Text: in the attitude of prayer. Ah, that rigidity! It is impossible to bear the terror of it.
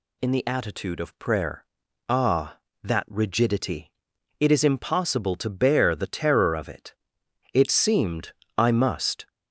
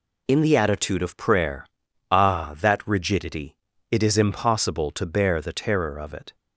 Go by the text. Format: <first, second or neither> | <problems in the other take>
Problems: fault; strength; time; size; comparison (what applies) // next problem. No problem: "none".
second | goes on to say "It seemed I must"; strong; from 7.5 s on; 1.7 s long